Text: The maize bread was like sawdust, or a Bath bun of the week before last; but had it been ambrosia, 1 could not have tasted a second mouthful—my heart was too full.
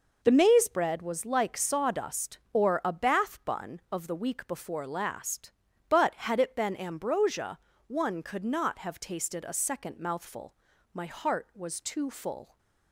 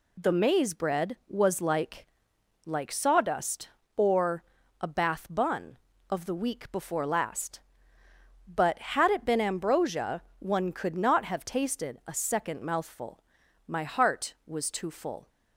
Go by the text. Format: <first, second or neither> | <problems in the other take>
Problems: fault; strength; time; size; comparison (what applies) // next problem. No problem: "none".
first | says "like" twice; at 2.6 s // pauses between "or" and "a"; at 4.4 s; 0.38 s long